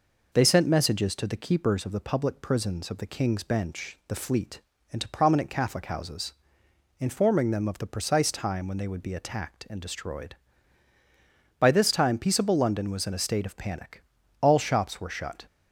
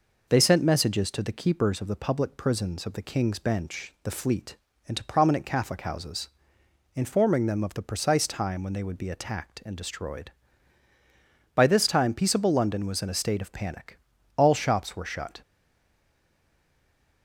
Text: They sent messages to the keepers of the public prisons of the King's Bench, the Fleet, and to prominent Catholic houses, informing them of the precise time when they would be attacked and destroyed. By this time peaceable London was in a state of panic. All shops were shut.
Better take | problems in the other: first | stays silent after the last word; noticeable; from 15.4 s on; 1.8 s long

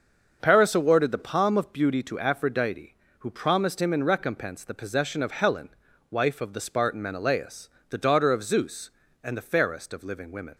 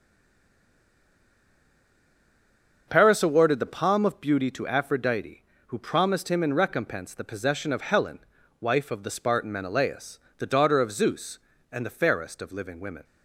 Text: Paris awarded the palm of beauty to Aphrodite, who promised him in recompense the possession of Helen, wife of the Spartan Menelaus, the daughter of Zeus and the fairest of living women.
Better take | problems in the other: first | stays silent before the first word; strong; until 2.8 s; 2.8 s long // starts louder than the rest; until 3.8 s; 6 dB; noticeable in the first

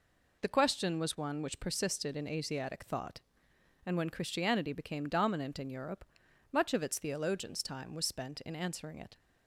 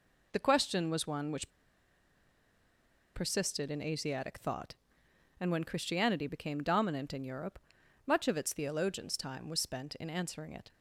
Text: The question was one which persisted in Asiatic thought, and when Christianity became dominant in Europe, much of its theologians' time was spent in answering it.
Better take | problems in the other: first | pauses between "which" and "persisted"; strong; at 1.4 s; 1.6 s long

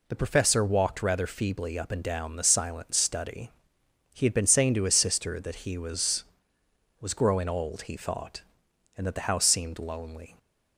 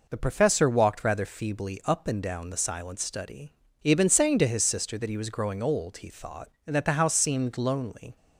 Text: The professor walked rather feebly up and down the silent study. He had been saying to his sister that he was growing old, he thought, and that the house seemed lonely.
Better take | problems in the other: second | says "was" twice; at 6.9 s

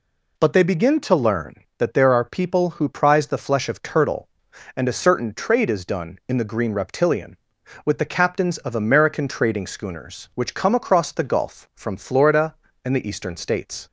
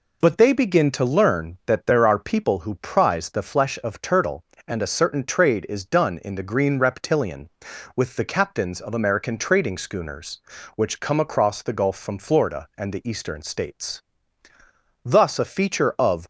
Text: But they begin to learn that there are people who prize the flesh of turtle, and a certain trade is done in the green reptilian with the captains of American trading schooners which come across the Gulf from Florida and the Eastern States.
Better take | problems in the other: first | goes on to say "Thus a feature of"; noticeable; from 15.0 s on; 1.2 s long

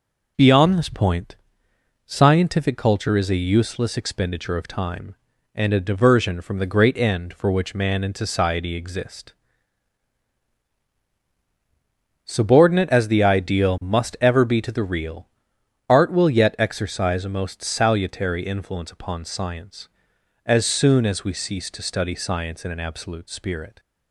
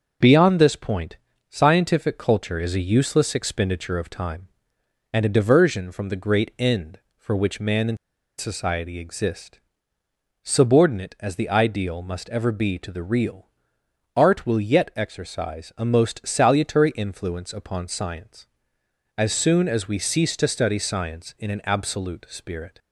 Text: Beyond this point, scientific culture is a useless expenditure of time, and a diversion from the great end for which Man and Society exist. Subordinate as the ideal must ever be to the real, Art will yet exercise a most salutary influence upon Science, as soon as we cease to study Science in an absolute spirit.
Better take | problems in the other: first | starts louder than the rest; noticeable; until 1.5 s; 6 dB // pauses between "and" and "Society"; at 7.9 s; 0.41 s long

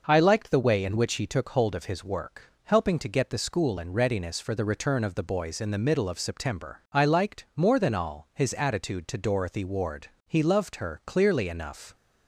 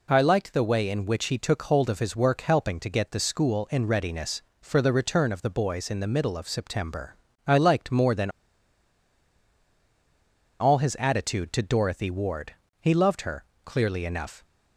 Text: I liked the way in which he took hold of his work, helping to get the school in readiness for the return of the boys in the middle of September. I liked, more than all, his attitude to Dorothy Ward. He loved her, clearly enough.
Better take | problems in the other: first | pauses between "than" and "all"; strong; at 8.3 s; 2.2 s long

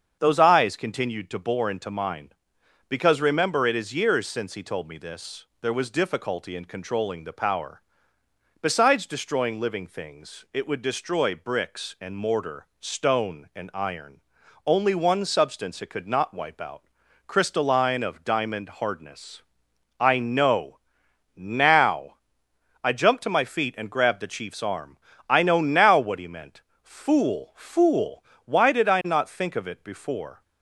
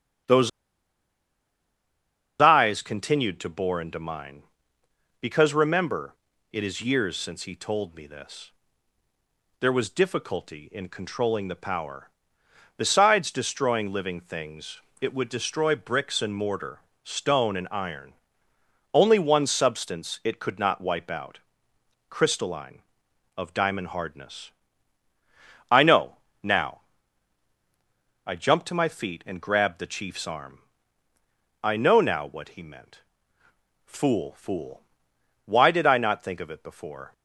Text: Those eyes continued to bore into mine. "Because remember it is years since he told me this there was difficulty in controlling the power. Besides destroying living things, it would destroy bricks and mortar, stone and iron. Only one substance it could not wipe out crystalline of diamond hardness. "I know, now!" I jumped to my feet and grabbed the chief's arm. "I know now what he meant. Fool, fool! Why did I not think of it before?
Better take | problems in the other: first | starts louder than the rest; strong; until 3.2 s; 8 dB; strong in the first // pauses between "Those" and "eyes"; strong; at 0.4 s; 1.9 s long // pauses between "remember" and "it"; slight; at 6.1 s; 0.36 s long // pauses between "this" and "there"; at 8.5 s; 1.1 s long; slight in the first // pauses between "out" and "crystalline"; noticeable; at 21.3 s; 0.72 s long; also in the first

